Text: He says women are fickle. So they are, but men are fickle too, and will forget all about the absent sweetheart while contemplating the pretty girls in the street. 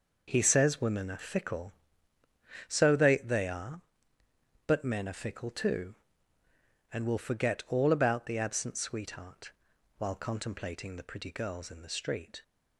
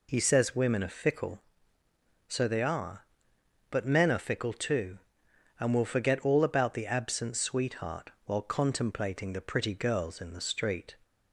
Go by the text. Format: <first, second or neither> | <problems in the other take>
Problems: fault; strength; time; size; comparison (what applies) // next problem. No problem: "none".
second | says "they" twice; at 3.1 s // pauses between "sweetheart" and "while"; at 9.5 s; 0.44 s long; slight in the second